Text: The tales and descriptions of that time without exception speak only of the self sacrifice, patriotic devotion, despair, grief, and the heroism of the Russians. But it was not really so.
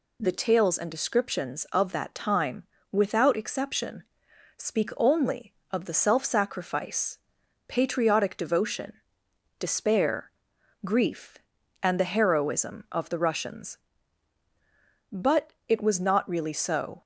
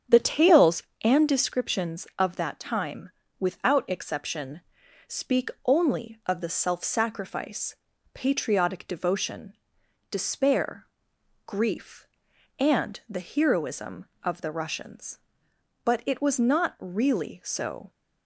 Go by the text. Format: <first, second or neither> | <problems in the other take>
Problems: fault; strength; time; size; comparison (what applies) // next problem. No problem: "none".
first | starts louder than the rest; strong; until 1.3 s; 8 dB // pauses between "time" and "without"; slight; at 3.0 s; 0.30 s long; slight in the first // pauses between "exception" and "speak"; noticeable; at 4.5 s; 0.48 s long; noticeable in the first // pauses between "speak" and "only"; slight; at 5.4 s; 0.16 s long